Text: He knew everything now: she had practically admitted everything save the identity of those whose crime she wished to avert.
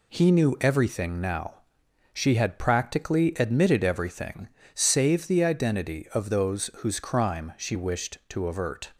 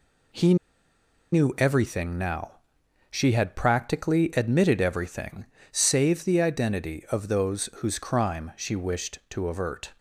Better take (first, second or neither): first